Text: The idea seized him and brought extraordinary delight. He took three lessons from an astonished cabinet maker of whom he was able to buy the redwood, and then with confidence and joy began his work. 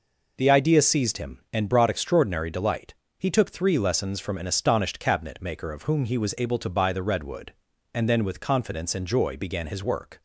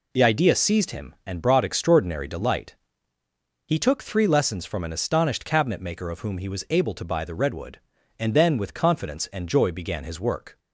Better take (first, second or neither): neither